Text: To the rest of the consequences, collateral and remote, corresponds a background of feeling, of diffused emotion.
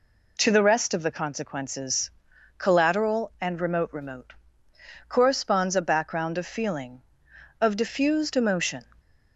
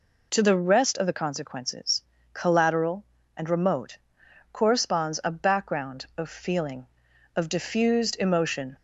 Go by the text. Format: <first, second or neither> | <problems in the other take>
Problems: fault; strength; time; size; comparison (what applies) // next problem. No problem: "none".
second | says "remote" twice; at 3.9 s